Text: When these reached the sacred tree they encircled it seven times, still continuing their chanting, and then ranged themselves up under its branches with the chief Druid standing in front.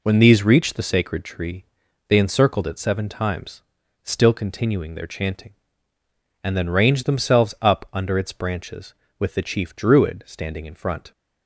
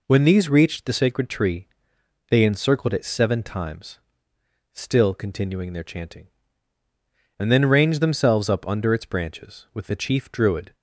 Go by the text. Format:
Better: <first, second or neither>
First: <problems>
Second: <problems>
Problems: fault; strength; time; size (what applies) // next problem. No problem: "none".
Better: first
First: pauses between "tree" and "they"; at 1.6 s; 0.42 s long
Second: pauses between "tree" and "they"; noticeable; at 1.6 s; 0.64 s long // stops before "standing in front"; at 10.7 s